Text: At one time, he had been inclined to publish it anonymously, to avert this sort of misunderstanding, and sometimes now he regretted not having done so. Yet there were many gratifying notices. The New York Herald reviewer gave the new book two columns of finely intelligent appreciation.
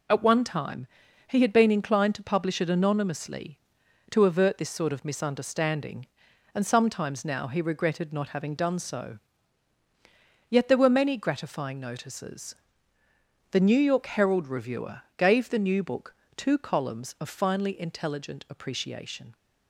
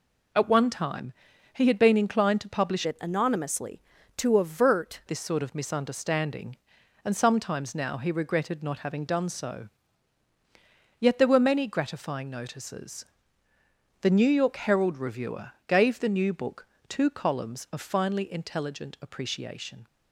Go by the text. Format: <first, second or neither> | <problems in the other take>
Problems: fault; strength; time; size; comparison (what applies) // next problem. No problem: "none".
first | changes voice from "it" to "avert"; from 2.8 to 5.0 s; 2.2 s long // pauses between "reviewer" and "gave"; slight; at 15.5 s; 0.16 s long; slight in the first // pauses between "book" and "two"; slight; at 16.6 s; 0.20 s long; slight in the first